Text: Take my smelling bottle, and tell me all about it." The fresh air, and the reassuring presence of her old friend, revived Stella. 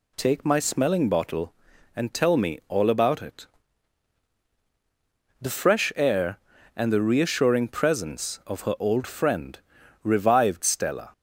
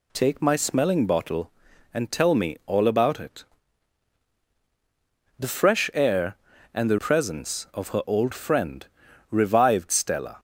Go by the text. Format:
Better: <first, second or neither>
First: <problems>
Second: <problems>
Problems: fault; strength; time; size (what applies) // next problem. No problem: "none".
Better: first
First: none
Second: skips "reassuring"; at 6.9 s